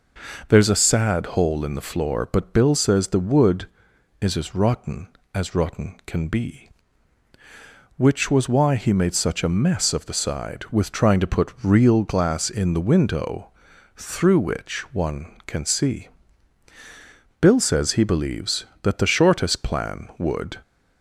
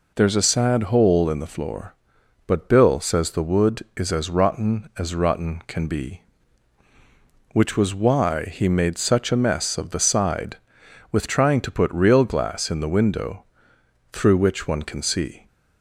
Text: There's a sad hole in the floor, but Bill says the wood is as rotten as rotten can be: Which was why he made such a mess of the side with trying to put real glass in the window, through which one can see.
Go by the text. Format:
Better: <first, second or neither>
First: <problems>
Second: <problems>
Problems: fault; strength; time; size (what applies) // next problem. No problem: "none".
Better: second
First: goes on to say "Bill says he believes that the shortest plan would"; strong; from 17.3 s on; 3.2 s long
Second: none